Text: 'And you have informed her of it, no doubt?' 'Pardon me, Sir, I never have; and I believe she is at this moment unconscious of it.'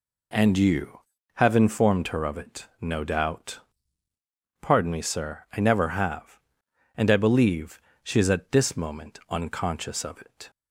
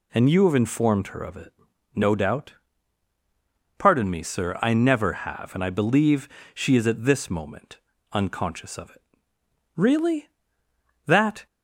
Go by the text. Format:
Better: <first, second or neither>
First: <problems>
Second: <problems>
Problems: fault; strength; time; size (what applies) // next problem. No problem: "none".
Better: first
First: pauses between "believe" and "she"; slight; at 7.8 s; 0.20 s long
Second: pauses between "believe" and "she"; slight; at 6.2 s; 0.26 s long // pauses between "moment" and "unconscious"; slight; at 7.7 s; 0.34 s long // goes on to say "Really that"; strong; from 9.7 s on; 1.7 s long